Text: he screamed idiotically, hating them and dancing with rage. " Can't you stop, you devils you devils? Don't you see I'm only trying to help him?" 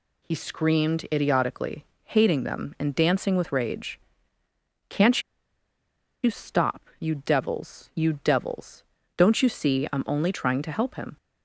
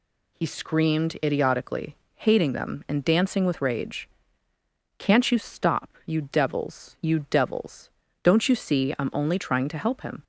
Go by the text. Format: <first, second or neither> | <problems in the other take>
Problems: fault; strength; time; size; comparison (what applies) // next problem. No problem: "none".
second | pauses between "Can't" and "you"; at 5.2 s; 1.0 s long